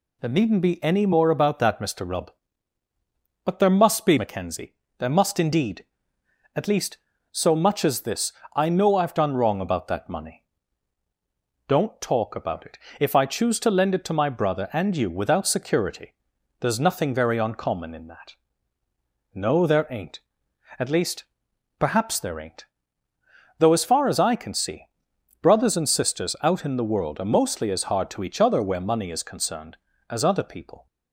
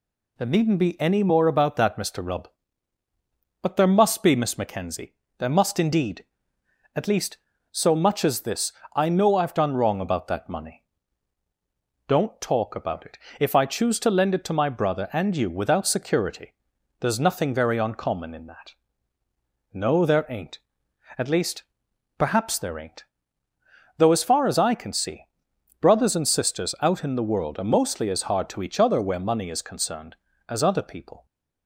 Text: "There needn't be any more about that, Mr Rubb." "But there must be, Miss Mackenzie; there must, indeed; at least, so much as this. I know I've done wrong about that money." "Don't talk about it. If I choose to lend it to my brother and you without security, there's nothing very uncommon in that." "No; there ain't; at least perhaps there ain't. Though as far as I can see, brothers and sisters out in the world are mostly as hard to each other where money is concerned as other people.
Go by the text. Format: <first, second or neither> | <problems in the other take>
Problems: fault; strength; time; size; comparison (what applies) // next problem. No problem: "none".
second | skips "Miss"; at 4.1 s // pauses between "least" and "perhaps"; noticeable; at 21.2 s; 0.54 s long; noticeable in the second